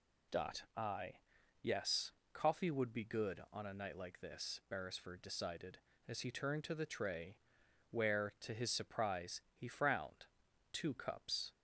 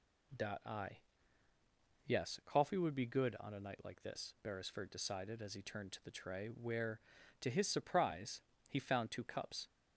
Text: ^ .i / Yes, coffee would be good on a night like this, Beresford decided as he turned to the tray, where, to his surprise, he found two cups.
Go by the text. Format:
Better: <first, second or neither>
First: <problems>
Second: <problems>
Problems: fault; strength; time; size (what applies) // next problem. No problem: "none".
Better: second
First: says "frowned" for "found"; at 9.6 s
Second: none